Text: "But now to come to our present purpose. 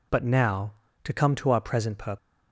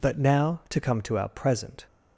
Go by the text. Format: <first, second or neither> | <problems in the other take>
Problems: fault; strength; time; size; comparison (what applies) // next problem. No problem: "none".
first | stops before "purpose"; at 1.8 s